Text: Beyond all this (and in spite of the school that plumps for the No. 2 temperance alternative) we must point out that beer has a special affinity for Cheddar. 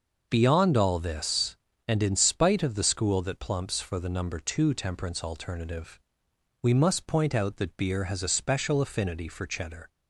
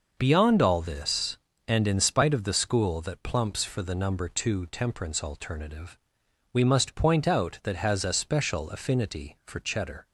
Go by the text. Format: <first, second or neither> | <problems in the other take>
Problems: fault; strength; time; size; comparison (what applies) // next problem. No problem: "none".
first | skips "beer"; at 7.7 s